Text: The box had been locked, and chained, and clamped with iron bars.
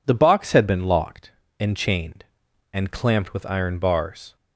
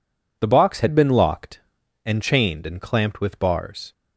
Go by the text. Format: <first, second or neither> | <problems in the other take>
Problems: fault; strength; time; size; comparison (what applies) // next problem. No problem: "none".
first | skips "iron"; at 3.4 s